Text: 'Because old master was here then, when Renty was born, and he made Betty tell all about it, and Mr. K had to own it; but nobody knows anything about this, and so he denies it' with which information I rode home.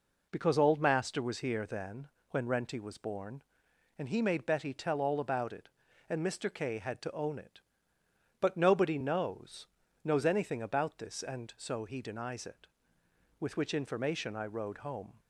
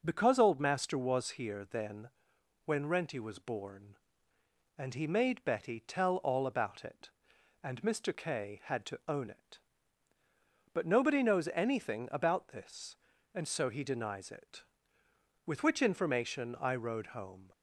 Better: second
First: says "knows" twice; at 10.0 s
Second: none

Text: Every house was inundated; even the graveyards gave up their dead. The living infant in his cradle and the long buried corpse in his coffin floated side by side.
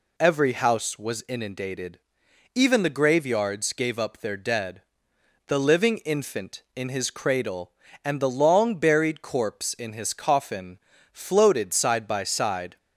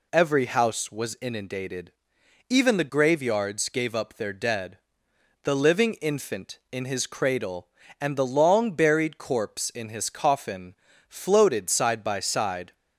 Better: neither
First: pauses between "coffin" and "floated"; slight; at 10.7 s; 0.32 s long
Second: pauses between "coffin" and "floated"; slight; at 10.7 s; 0.32 s long

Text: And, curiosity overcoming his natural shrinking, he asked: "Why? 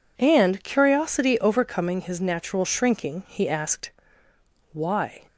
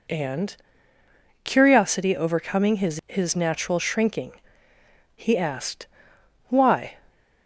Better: first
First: none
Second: says "his" twice; at 3.0 s

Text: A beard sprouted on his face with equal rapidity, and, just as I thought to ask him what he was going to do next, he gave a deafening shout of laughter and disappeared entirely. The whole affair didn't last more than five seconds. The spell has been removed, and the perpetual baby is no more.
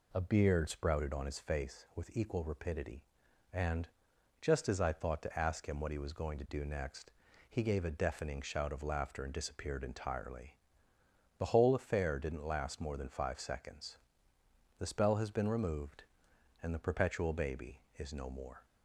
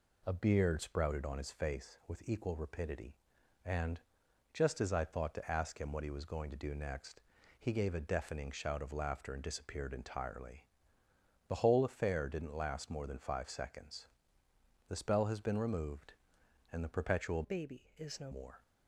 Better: first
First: none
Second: changes voice from "baby" to "no"; from 17.4 to 18.3 s; 0.9 s long

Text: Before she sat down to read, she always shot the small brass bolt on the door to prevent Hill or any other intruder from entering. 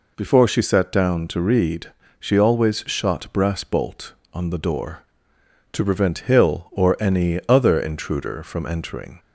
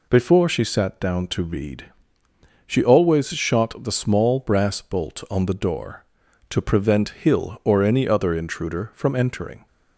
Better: second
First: skips "the small"; at 3.3 s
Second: none

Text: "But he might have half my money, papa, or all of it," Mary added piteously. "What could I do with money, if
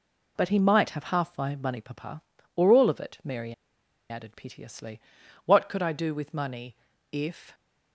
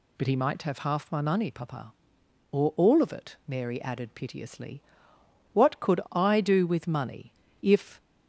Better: second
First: pauses between "Mary" and "added"; noticeable; at 3.5 s; 0.55 s long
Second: none

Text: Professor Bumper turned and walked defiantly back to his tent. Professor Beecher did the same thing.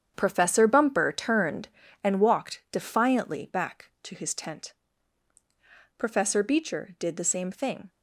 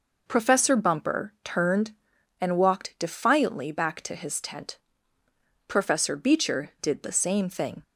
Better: second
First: gets quieter; strong; throughout; 10 dB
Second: none

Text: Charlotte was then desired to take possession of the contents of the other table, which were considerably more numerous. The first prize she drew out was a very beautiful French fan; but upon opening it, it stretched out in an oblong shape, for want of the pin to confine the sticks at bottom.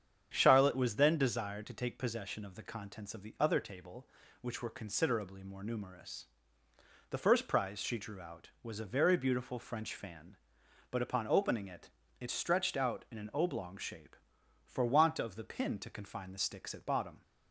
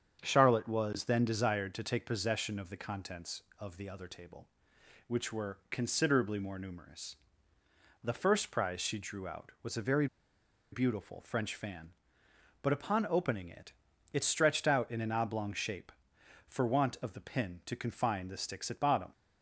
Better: first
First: starts louder than the rest; strong; until 1.3 s; 8 dB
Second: starts louder than the rest; strong; until 1.2 s; 7.5 dB // pauses between "very" and "beautiful"; noticeable; at 10.0 s; 0.66 s long

